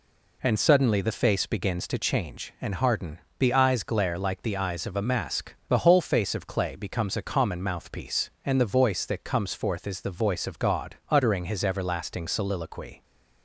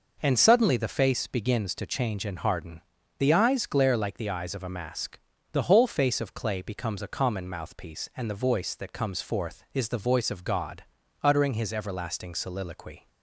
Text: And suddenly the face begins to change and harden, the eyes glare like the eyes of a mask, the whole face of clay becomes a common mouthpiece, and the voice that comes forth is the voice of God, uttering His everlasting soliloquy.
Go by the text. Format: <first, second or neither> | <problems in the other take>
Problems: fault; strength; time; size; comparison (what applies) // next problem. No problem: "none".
neither | none